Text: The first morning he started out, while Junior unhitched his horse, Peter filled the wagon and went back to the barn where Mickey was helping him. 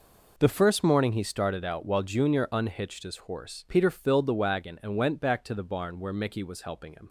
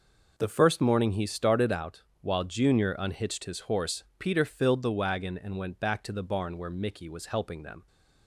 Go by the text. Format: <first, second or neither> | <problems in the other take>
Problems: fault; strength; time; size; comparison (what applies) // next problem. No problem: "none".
first | says "them" for "him"; at 7.6 s